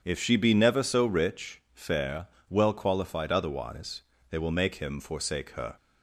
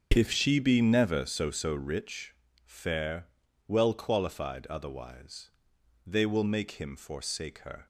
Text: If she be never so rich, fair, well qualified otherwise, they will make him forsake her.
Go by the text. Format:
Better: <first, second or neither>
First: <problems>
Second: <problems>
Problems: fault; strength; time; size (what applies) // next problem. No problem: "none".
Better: first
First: starts louder than the rest; strong; until 1.0 s; 8 dB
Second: starts louder than the rest; until 1.1 s; 7 dB // says "so" twice; at 1.5 s